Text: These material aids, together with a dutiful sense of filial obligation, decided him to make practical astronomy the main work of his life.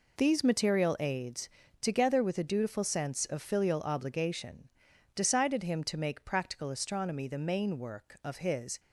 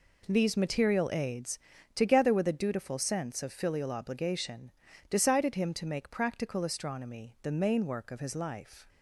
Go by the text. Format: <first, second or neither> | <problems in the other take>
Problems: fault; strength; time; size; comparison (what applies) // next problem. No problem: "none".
second | stops before "life"; at 8.7 s